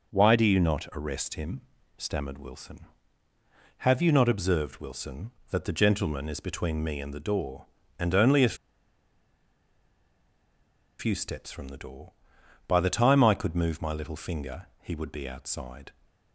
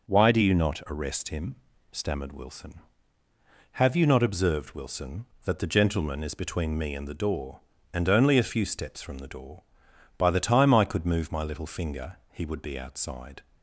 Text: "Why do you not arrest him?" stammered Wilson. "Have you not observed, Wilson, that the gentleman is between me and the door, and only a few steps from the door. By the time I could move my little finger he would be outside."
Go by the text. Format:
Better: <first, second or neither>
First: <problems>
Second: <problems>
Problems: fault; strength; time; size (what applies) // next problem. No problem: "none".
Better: second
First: pauses between "a" and "few"; strong; at 8.5 s; 2.4 s long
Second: none